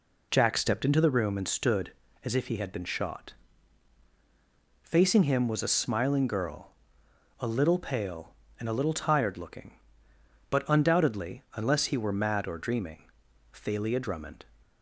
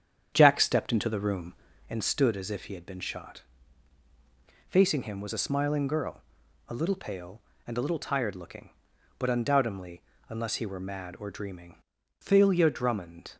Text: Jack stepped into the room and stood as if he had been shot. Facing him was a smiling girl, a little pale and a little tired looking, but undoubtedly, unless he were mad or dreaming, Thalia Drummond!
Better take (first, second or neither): first